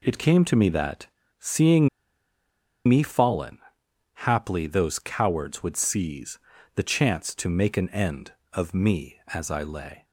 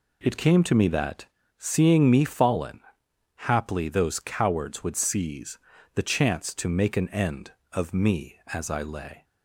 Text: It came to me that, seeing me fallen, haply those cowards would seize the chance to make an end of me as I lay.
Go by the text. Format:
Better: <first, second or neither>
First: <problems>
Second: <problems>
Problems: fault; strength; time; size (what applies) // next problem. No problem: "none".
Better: second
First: pauses between "seeing" and "me"; at 1.8 s; 0.99 s long // pauses between "seize" and "the"; slight; at 6.3 s; 0.36 s long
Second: pauses between "seize" and "the"; slight; at 5.5 s; 0.36 s long